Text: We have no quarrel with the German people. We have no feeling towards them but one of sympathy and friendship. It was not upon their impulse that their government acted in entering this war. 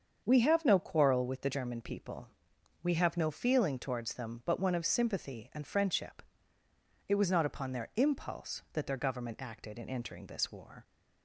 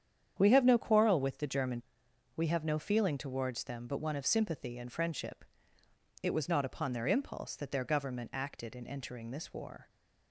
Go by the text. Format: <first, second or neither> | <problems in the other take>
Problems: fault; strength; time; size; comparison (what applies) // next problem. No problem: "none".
first | starts louder than the rest; strong; until 1.4 s; 8.5 dB; also in the first // skips "people"; at 2.0 s